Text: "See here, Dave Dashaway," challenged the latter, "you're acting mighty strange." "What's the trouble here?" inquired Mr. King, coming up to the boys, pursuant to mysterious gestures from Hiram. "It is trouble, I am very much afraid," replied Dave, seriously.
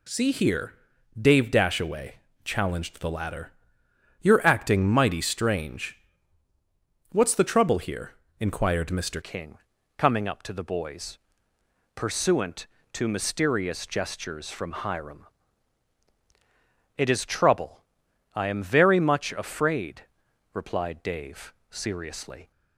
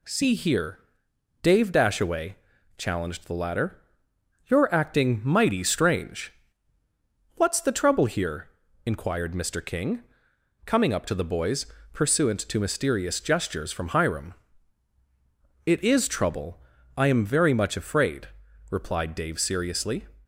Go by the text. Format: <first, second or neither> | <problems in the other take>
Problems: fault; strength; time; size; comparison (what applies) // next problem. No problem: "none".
second | changes voice at "King"; from 9.2 s on; 13.3 s long